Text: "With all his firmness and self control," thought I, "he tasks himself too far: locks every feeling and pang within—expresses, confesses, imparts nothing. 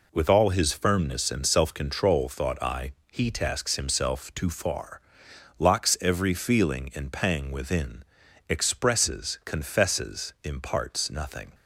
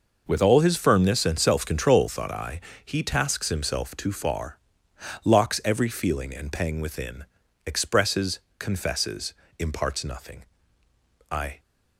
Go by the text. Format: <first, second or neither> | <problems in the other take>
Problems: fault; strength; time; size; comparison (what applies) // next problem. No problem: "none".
first | goes on to say "I"; slight; from 11.3 s on; 0.28 s long